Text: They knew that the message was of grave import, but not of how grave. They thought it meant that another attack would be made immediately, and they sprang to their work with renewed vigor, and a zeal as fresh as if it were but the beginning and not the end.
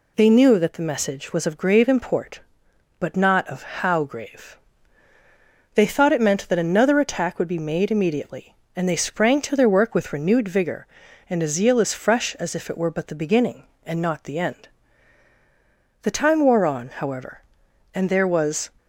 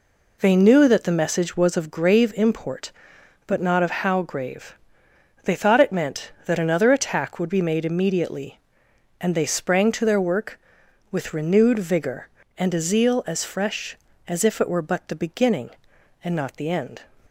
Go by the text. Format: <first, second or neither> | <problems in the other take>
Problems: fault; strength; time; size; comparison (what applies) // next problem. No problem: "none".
second | goes on to say "The time wore on however and there was"; strong; from 16.0 s on; 2.6 s long